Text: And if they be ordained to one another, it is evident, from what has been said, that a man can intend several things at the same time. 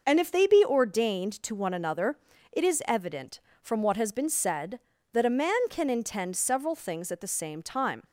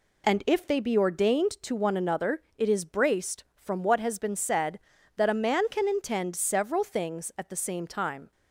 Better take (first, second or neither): first